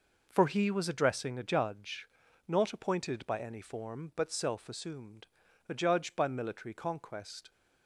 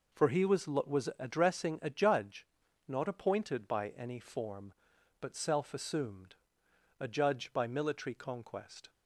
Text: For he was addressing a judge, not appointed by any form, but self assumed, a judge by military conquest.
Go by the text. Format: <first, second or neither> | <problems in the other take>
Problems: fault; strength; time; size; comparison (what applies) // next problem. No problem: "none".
first | says "was" twice; at 0.6 s